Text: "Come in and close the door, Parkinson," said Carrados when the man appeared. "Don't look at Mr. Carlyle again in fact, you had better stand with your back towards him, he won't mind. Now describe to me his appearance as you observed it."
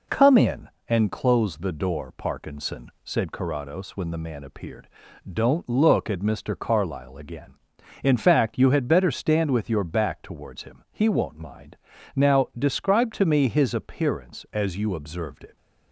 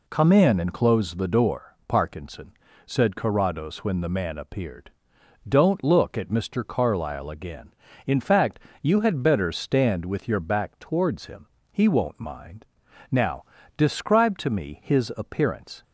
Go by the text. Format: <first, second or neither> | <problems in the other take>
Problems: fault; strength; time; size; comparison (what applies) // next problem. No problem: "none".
first | pauses between "Now" and "describe"; slight; at 13.4 s; 0.34 s long // stops before "as you observed it"; at 15.8 s